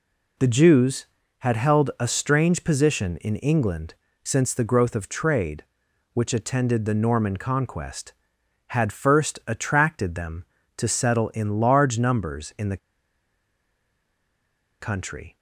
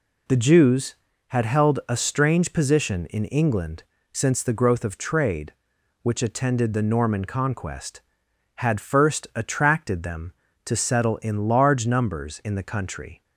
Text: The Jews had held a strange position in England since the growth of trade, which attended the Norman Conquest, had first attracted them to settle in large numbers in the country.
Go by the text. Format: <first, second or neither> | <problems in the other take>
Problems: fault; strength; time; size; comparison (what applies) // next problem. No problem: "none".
second | pauses between "England" and "since"; slight; at 3.9 s; 0.28 s long; slight in the second // pauses between "the" and "country"; strong; at 12.7 s; 2.0 s long